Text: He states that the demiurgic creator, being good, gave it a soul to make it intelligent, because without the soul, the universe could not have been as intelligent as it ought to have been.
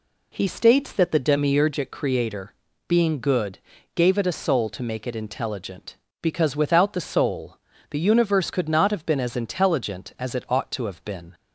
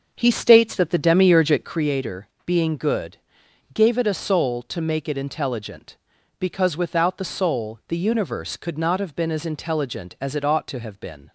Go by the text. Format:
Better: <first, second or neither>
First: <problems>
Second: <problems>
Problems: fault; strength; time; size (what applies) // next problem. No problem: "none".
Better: first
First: none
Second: starts louder than the rest; until 1.9 s; 6.5 dB